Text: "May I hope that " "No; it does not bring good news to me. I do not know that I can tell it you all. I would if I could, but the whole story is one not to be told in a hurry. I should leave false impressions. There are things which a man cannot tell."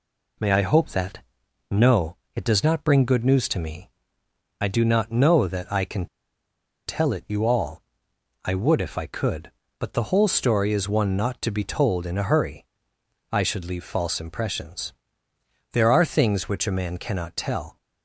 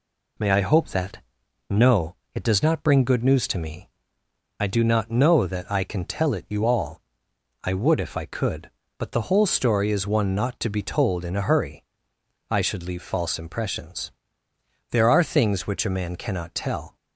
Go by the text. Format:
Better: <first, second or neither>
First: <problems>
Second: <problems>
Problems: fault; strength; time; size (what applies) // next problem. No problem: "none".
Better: second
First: pauses between "can" and "tell"; noticeable; at 6.0 s; 0.80 s long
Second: none